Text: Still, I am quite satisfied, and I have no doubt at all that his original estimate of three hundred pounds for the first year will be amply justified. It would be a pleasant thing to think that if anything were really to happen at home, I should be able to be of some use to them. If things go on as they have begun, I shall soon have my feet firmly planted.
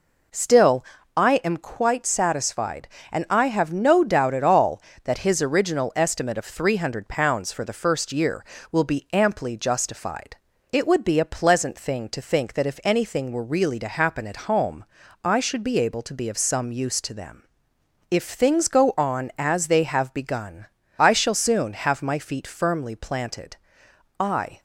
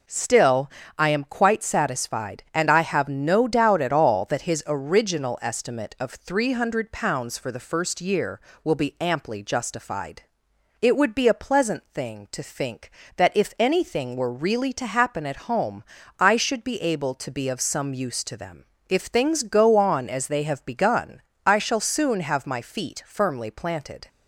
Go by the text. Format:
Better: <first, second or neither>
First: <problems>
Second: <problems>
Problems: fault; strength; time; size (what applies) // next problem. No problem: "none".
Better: second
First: goes on to say "I"; slight; from 24.1 s on; 0.40 s long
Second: none